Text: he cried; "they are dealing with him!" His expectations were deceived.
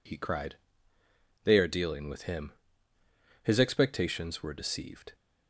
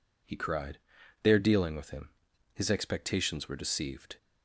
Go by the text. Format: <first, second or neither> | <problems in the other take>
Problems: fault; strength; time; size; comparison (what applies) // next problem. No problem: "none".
neither | none